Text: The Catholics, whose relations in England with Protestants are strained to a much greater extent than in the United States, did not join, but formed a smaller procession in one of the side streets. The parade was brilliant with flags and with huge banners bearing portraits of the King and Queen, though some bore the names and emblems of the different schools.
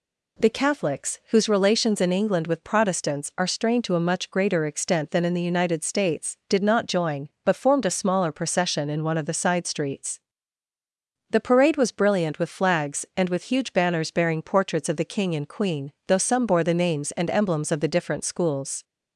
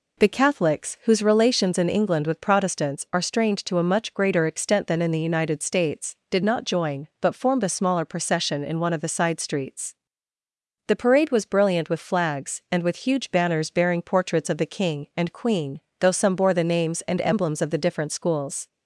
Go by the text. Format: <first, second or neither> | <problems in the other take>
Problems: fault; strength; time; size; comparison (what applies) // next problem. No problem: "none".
neither | none